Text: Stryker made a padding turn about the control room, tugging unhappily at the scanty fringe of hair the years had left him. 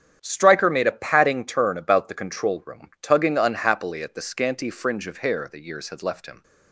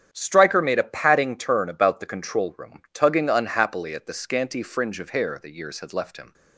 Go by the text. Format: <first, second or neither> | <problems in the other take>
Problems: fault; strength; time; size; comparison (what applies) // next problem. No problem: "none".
neither | starts louder than the rest; strong; the same in both